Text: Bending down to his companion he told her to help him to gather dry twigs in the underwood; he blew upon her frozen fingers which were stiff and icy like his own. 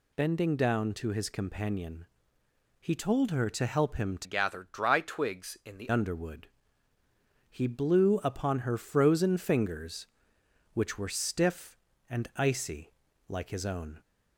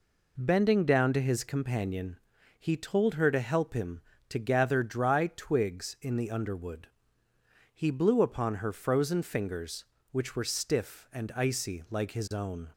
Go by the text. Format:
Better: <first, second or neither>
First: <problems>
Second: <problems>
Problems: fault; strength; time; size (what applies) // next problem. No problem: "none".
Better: second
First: pauses between "companion" and "he"; noticeable; at 2.0 s; 0.74 s long // changes voice from "gather" to "the"; from 4.2 to 5.8 s; 1.6 s long // pauses between "icy" and "like"; slight; at 12.9 s; 0.36 s long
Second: pauses between "companion" and "he"; at 2.1 s; 0.40 s long